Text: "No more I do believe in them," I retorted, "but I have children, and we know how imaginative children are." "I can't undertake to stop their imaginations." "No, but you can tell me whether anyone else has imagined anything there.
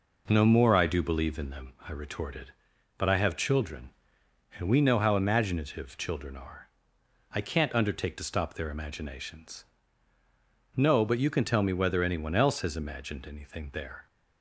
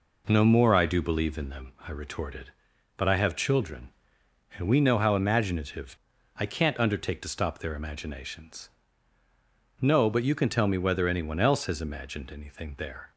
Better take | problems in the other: first | skips "children are"; at 6.1 s

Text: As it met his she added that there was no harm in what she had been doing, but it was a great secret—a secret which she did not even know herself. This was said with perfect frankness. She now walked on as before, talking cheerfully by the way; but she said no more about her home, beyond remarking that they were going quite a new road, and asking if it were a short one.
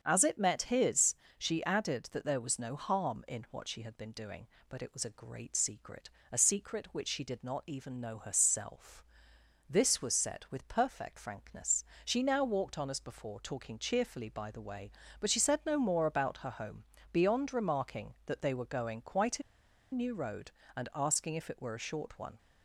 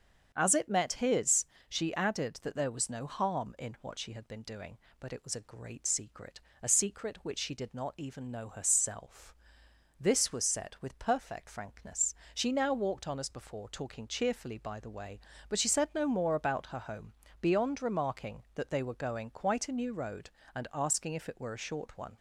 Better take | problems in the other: second | starts louder than the rest; until 1.0 s; 7 dB; also in the second // pauses between "his" and "she"; slight; at 1.1 s; 0.24 s long; slight in the second // pauses between "a" and "new"; noticeable; at 19.4 s; 0.51 s long

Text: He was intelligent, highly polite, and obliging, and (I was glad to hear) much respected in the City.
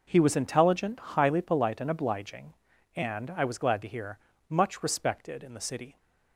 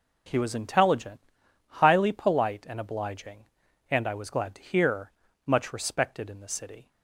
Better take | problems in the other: neither | none

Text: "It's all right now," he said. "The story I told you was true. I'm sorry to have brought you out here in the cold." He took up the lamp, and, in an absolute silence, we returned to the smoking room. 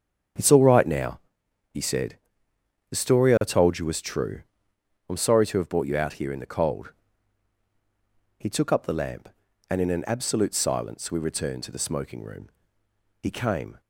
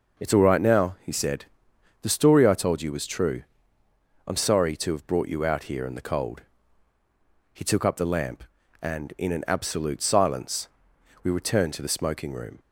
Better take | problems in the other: second | starts louder than the rest; strong; until 1.9 s; 8 dB // goes on to say "He came"; from 13.2 s on; 0.60 s long

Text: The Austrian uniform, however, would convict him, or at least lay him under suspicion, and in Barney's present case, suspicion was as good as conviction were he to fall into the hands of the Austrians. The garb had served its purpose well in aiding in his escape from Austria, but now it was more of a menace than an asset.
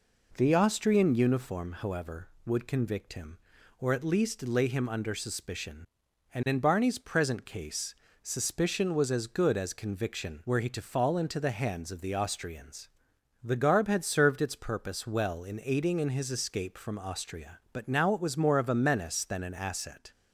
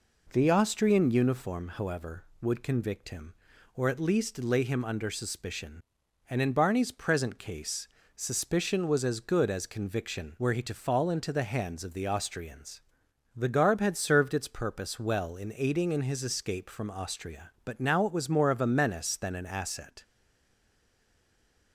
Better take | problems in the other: first | stays silent after the last word; noticeable; from 20.0 s on; 1.7 s long

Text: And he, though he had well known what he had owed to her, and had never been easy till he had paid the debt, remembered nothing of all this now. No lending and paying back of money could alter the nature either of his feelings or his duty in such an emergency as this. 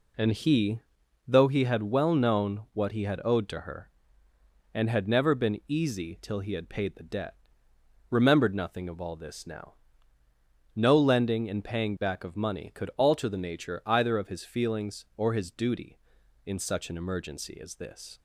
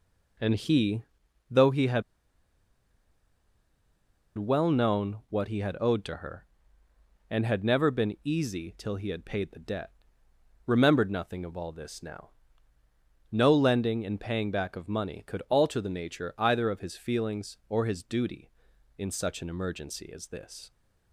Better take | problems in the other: first | pauses between "had" and "well"; strong; at 2.0 s; 2.3 s long

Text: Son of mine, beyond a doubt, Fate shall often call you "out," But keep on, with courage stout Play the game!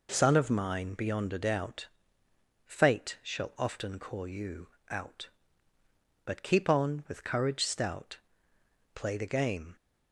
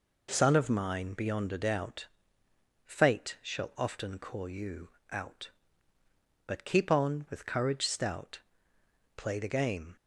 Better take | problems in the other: neither | pauses between "you" and "out"; slight; the same in both // pauses between "stout" and "Play"; noticeable; the same in both

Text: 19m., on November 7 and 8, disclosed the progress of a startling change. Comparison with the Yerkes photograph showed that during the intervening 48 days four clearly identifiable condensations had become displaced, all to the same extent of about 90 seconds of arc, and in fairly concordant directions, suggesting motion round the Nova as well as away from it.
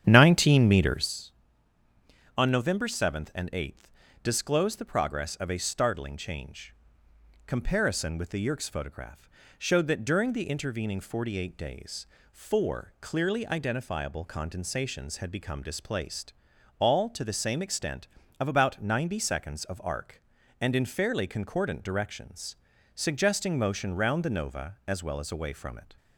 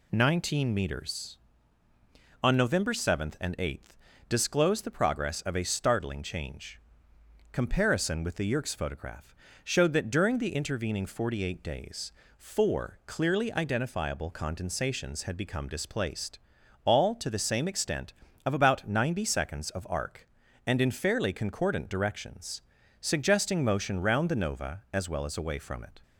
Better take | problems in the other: second | starts louder than the rest; strong; until 1.2 s; 9 dB // pauses between "photograph" and "showed"; slight; at 9.3 s; 0.28 s long; slight in the second // pauses between "days" and "four"; slight; at 12.0 s; 0.26 s long; slight in the second

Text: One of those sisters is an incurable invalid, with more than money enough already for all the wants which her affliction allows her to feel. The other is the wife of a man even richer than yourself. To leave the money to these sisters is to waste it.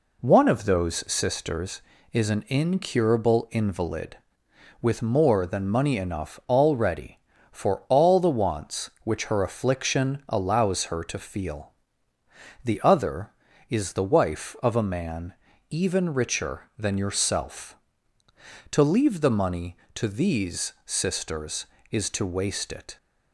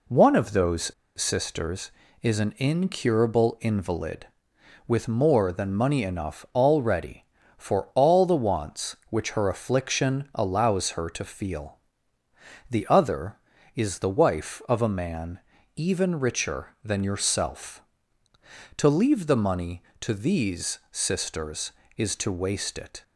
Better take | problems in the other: first | pauses between "those" and "sisters"; slight; at 0.9 s; 0.24 s long // pauses between "man" and "even"; at 15.3 s; 0.38 s long; also in the first

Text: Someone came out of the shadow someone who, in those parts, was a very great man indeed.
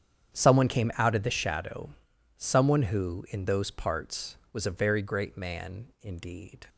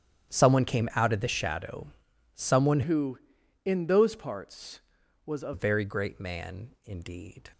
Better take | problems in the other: first | starts louder than the rest; strong; until 1.3 s; 9.5 dB; strong in the first // pauses between "shadow" and "someone"; noticeable; at 1.8 s; 0.48 s long; noticeable in the first // changes voice from "who" to "a"; from 2.8 to 5.5 s; 2.7 s long // pauses between "man" and "indeed"; slight; at 6.6 s; 0.16 s long; slight in the first

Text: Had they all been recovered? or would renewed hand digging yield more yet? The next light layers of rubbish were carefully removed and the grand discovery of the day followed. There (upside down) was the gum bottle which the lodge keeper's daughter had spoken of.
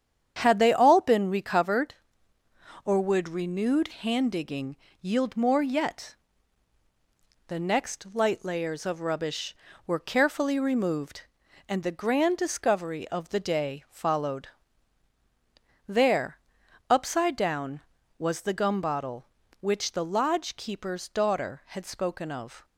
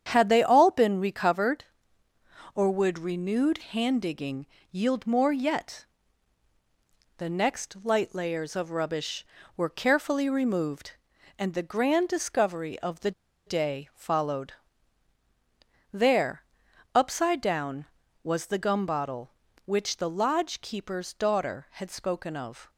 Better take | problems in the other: first | starts louder than the rest; strong; until 1.1 s; 8.5 dB; strong in the first // pauses between "digging" and "yield"; slight; at 4.4 s; 0.24 s long; slight in the first // pauses between "the" and "day"; slight; at 13.1 s; 0.35 s long

